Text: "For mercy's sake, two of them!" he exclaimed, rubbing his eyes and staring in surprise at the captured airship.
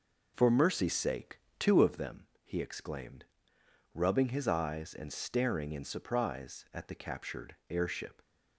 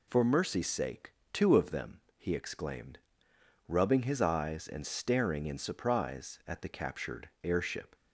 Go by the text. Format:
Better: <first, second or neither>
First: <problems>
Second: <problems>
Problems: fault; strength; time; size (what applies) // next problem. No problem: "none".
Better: second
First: starts louder than the rest; noticeable; until 1.9 s; 5 dB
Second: none